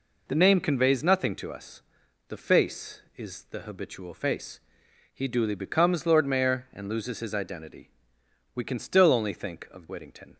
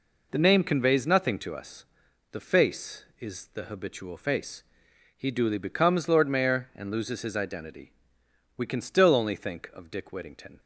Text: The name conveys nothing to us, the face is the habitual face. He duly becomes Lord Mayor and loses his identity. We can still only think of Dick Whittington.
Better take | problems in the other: second | skips "Dick"; at 9.8 s

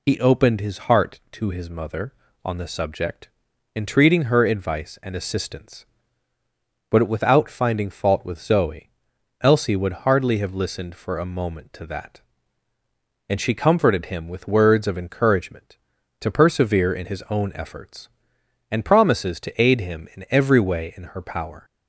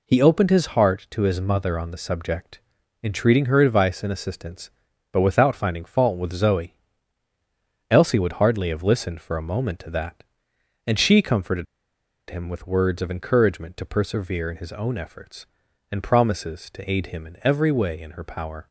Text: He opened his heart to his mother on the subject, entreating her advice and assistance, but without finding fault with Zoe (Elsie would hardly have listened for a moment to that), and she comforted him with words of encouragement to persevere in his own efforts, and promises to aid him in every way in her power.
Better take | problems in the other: first | pauses between "comforted" and "him"; noticeable; at 11.6 s; 0.65 s long

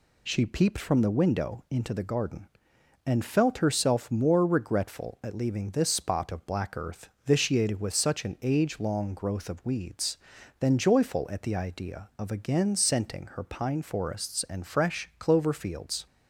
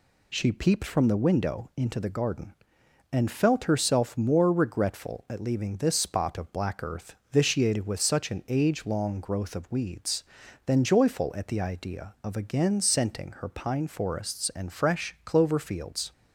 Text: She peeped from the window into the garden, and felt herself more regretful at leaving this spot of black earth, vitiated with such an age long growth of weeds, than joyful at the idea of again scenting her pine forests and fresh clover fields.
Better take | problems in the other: neither | none

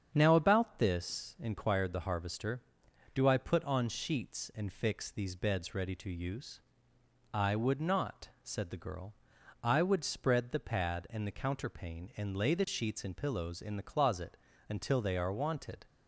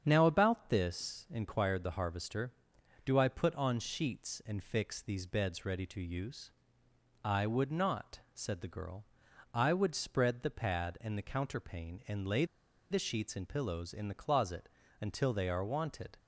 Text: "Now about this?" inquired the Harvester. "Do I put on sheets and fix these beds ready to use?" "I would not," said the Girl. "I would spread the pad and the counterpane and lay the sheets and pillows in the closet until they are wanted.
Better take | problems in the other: first | starts louder than the rest; strong; until 1.0 s; 8 dB; strong in the first // pauses between "lay" and "the"; noticeable; at 12.4 s; 0.46 s long // pauses between "closet" and "until"; slight; at 14.6 s; 0.34 s long; slight in the first

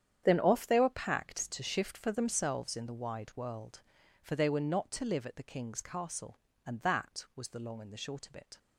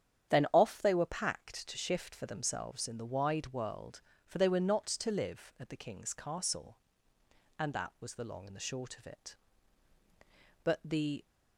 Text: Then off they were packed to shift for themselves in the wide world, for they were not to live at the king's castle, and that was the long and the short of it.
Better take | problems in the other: first | starts louder than the rest; strong; until 1.3 s; 9.5 dB; strong in the first // goes on to say "But the"; noticeable; from 10.6 s on; 0.62 s long

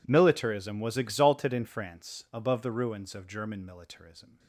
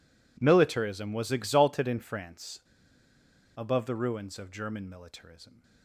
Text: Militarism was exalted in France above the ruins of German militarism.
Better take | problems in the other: first | pauses between "France" and "above"; noticeable; at 2.6 s; 0.96 s long

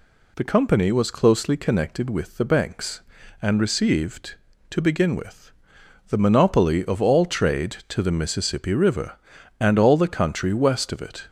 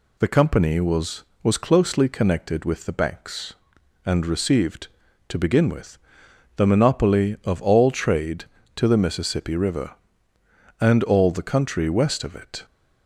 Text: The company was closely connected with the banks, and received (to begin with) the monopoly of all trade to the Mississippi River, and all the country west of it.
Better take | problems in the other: first | says "was" twice; at 1.4 s

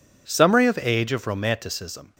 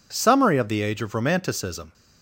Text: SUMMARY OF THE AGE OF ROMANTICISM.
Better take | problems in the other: second | skips "THE"; at 0.7 s

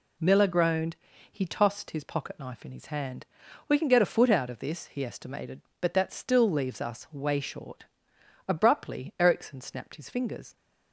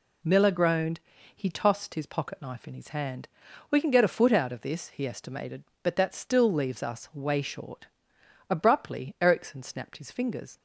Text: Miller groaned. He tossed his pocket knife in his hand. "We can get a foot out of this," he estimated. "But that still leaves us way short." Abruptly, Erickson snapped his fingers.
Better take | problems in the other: neither | none

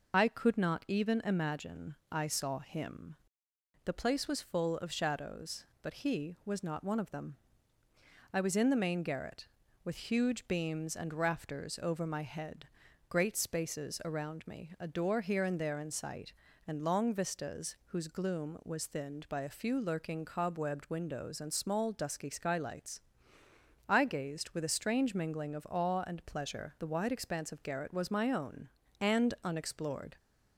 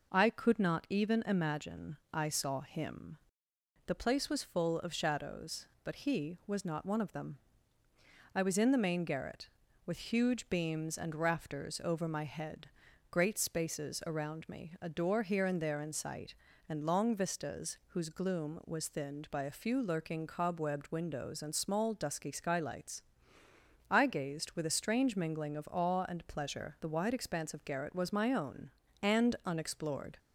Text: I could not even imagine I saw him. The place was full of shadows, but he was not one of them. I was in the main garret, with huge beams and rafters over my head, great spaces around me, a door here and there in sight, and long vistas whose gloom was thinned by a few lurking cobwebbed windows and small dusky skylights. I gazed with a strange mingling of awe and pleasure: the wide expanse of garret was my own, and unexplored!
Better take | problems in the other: second | loses the start of "I"; at 0.1 s; 50 ms // pauses between "imagine" and "I"; slight; at 1.9 s; 0.16 s long; slight in the second

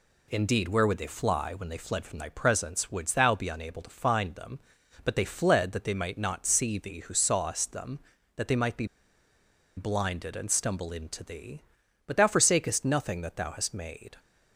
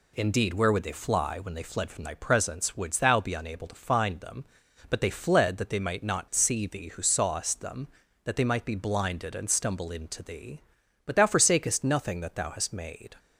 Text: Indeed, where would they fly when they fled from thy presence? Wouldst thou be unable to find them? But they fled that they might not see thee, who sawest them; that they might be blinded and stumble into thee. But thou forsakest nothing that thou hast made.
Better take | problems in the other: second | pauses between "be" and "blinded"; noticeable; at 8.8 s; 0.91 s long

